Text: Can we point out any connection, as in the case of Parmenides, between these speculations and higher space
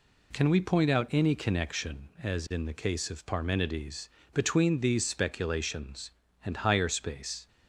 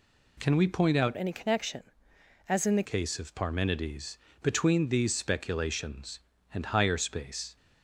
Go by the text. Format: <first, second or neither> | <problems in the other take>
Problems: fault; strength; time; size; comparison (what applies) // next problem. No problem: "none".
first | changes voice from "any" to "the"; from 1.1 to 2.8 s; 1.7 s long